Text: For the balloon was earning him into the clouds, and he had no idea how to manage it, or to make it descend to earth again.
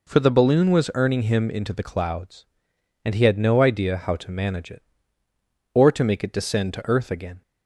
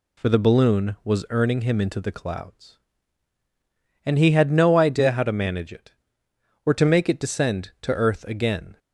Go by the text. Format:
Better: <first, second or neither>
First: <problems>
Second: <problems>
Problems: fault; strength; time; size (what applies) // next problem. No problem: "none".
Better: neither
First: none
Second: none